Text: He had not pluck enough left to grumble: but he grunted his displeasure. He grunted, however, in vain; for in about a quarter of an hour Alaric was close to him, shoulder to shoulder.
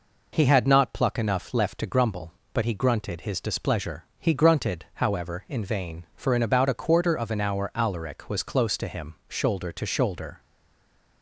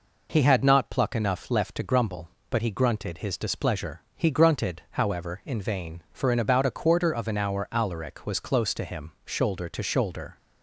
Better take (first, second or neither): second